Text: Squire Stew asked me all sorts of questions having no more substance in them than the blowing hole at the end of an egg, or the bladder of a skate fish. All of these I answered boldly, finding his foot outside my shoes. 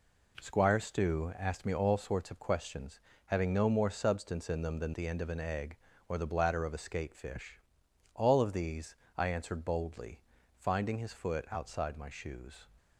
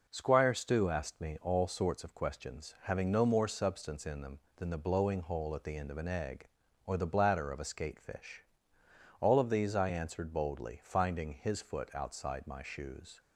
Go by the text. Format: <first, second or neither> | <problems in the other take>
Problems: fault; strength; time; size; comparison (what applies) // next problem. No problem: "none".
second | pauses between "questions" and "having"; slight; at 2.9 s; 0.26 s long // skips "the blowing hole at"; at 4.9 s // pauses between "these" and "I"; slight; at 8.9 s; 0.24 s long